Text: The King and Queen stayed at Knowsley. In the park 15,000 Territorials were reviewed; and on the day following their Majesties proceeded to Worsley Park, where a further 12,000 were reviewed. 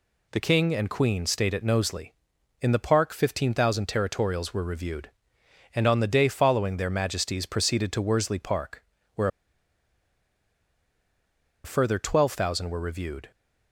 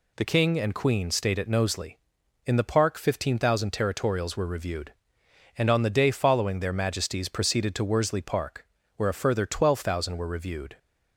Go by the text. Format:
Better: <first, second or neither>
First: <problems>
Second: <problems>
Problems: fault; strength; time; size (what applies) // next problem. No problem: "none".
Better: second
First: pauses between "where" and "a"; strong; at 9.2 s; 2.3 s long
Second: none